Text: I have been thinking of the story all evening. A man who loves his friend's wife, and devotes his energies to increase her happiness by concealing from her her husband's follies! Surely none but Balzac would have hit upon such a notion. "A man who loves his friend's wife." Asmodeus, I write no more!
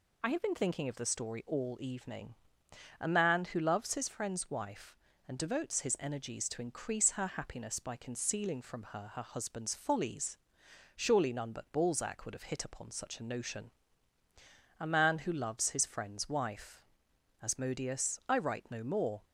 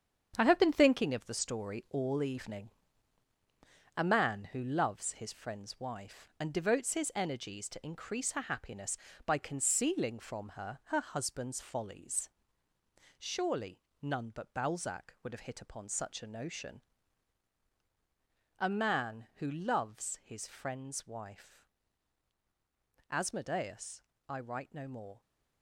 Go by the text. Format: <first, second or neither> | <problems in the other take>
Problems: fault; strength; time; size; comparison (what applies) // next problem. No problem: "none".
first | gets quieter; strong; throughout; 8 dB // pauses between "Surely" and "none"; slight; at 13.7 s; 0.24 s long